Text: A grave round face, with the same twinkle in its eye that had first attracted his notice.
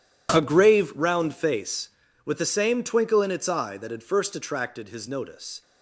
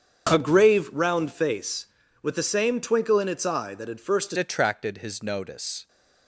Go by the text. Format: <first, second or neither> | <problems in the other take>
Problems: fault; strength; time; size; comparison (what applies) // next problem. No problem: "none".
first | starts louder than the rest; strong; until 1.3 s; 7.5 dB // changes voice at "attracted"; from 4.3 s on; 1.5 s long